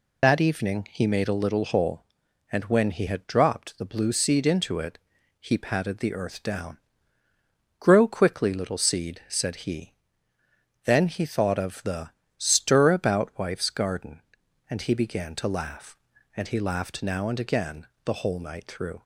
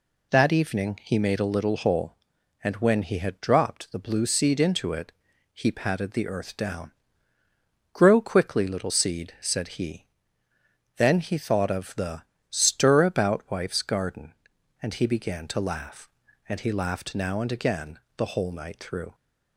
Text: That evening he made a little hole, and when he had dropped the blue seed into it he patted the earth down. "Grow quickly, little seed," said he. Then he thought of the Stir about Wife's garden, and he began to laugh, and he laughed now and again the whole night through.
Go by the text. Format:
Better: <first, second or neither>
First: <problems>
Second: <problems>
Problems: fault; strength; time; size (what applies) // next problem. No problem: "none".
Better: second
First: loses the start of "That"; at 0.2 s; 50 ms // pauses between "it" and "he"; at 4.9 s; 0.42 s long // pauses between "the" and "Stir"; slight; at 12.1 s; 0.28 s long // pauses between "again" and "the"; slight; at 17.8 s; 0.18 s long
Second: pauses between "it" and "he"; at 5.1 s; 0.42 s long // pauses between "the" and "Stir"; slight; at 12.2 s; 0.28 s long // pauses between "again" and "the"; slight; at 17.9 s; 0.18 s long